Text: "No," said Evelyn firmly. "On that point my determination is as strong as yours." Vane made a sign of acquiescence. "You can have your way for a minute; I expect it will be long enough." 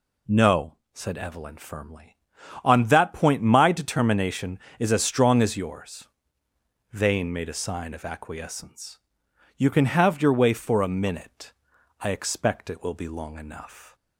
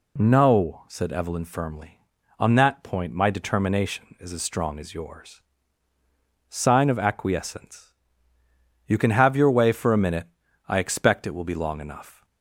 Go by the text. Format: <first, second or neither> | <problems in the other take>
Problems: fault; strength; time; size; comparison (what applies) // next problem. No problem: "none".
first | skips "Vane made a"; at 5.9 s